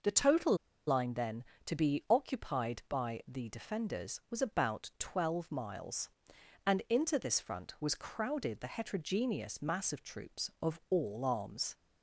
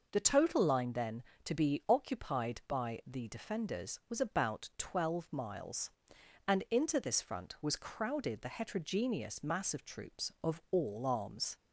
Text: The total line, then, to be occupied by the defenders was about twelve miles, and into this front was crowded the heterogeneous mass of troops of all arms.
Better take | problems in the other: second | pauses between "total" and "line"; slight; at 0.5 s; 0.32 s long

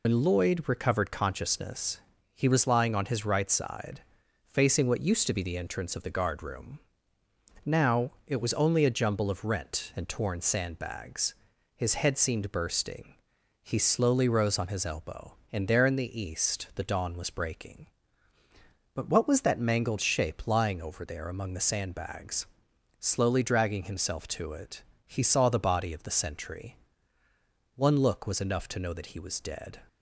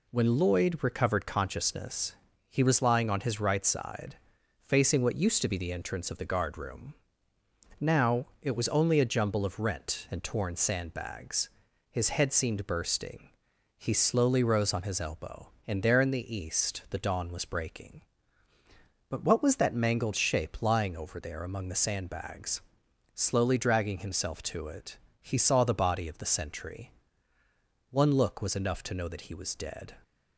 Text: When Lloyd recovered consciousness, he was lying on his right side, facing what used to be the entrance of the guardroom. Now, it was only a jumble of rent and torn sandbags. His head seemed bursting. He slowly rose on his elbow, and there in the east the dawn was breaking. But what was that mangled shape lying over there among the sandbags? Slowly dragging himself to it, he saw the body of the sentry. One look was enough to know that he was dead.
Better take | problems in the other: second | loses the start of "When"; at 0.0 s; 105 ms

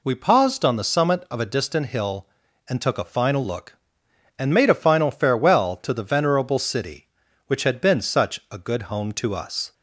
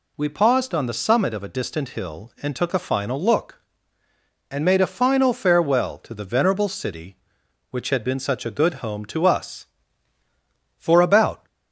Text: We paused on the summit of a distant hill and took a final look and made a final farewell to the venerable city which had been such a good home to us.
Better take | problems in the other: first | goes on to say "For about"; noticeable; from 10.7 s on; 0.68 s long

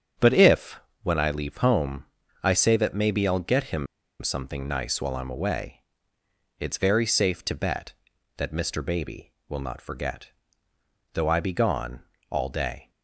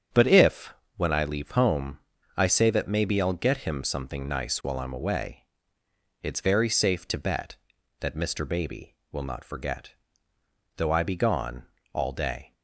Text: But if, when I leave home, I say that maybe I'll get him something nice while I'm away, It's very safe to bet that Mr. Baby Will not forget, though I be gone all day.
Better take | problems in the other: second | starts louder than the rest; strong; until 1.4 s; 7.5 dB; strong in the second // pauses between "him" and "something"; at 3.8 s; 0.36 s long // pauses between "gone" and "all"; slight; at 12.0 s; 0.28 s long; slight in the second

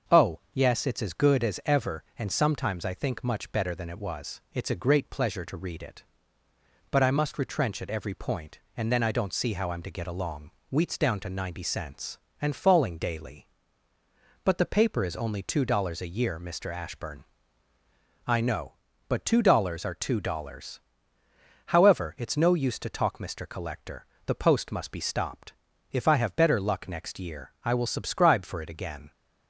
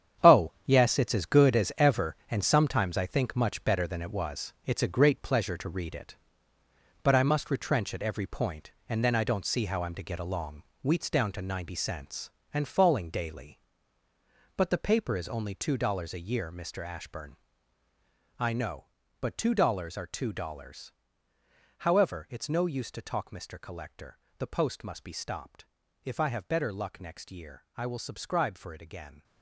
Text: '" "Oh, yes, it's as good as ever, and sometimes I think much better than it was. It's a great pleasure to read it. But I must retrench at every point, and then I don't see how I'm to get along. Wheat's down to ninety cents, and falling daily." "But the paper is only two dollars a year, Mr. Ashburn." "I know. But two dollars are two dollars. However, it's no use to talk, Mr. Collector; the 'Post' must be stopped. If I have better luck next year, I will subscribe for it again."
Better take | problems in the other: first | gets quieter; strong; throughout; 11.5 dB // starts louder than the rest; strong; until 1.3 s; 8.5 dB; also in the first

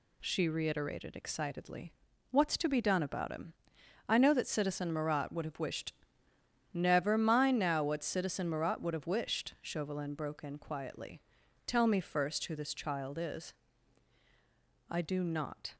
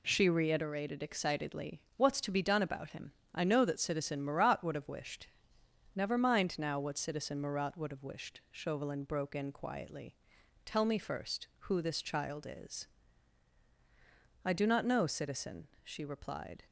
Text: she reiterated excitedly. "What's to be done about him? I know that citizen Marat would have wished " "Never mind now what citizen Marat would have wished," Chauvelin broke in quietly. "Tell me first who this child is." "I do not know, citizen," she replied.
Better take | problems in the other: second | stops before "know citizen she replied"; at 15.7 s

